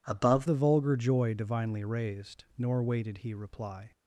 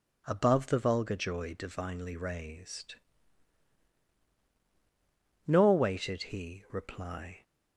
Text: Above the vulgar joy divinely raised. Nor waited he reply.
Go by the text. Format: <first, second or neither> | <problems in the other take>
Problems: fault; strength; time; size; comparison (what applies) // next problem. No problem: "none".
second | changes voice at "the"; from 0.4 s on; 3.5 s long